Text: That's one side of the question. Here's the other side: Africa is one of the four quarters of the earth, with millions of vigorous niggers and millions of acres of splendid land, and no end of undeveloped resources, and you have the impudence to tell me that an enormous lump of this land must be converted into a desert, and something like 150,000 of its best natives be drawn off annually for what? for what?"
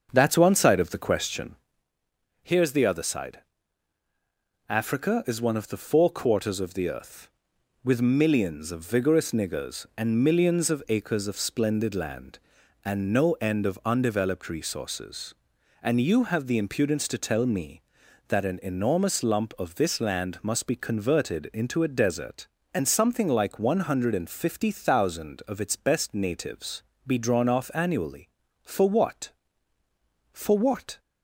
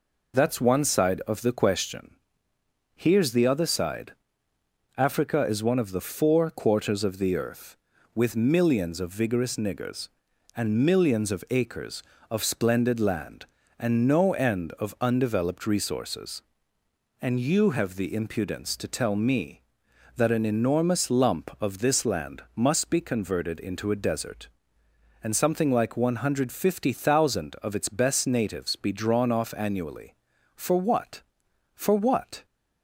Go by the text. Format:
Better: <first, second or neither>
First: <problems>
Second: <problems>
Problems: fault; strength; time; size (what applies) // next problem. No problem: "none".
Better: second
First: starts louder than the rest; until 1.9 s; 6.5 dB // pauses between "natives" and "be"; slight; at 26.8 s; 0.24 s long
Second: none